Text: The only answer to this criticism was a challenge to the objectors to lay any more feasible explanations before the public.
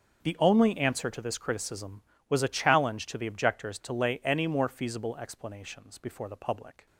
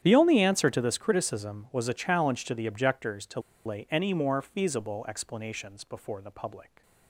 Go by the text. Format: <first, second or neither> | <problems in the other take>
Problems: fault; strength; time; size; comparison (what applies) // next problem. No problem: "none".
first | starts louder than the rest; strong; until 1.0 s; 10 dB; also in the first // pauses between "to" and "lay"; slight; at 3.3 s; 0.25 s long